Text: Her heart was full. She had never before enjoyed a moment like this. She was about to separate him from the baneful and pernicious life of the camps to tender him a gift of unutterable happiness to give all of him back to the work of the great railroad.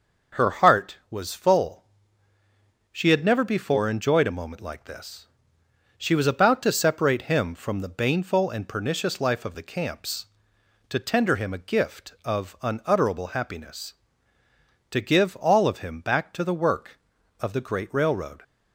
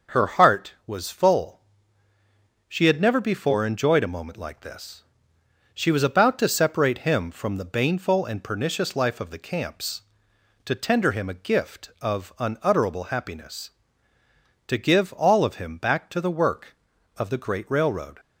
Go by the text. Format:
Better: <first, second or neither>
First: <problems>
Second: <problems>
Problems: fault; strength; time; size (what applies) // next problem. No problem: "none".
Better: neither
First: none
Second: none